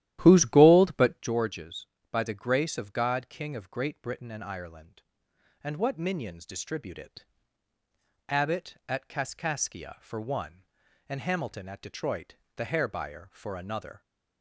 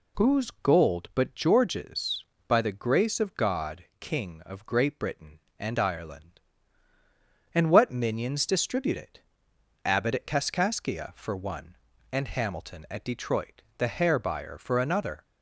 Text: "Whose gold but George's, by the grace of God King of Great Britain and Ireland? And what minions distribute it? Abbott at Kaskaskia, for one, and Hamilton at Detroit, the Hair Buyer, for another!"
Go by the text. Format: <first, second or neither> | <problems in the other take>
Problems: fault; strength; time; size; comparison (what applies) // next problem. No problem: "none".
second | starts louder than the rest; strong; until 1.4 s; 12.5 dB